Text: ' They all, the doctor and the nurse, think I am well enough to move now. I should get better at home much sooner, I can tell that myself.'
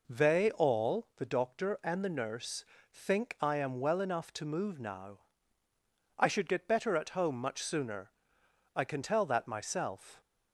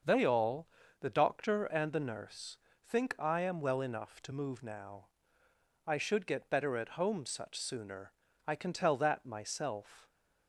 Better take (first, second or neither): first